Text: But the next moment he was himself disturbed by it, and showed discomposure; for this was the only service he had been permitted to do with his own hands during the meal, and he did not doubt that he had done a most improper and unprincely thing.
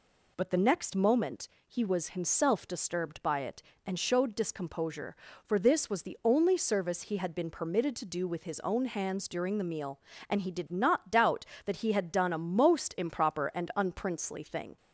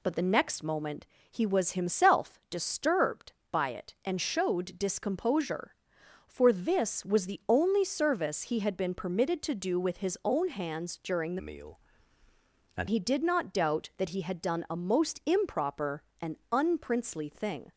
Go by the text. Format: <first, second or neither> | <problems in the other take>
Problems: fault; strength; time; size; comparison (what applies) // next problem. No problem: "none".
first | pauses between "moment" and "he"; slight; at 1.0 s; 0.24 s long; slight in the first // changes voice from "meal" to "and"; from 11.3 to 12.8 s; 1.5 s long // pauses between "and" and "unprincely"; slight; at 16.3 s; 0.16 s long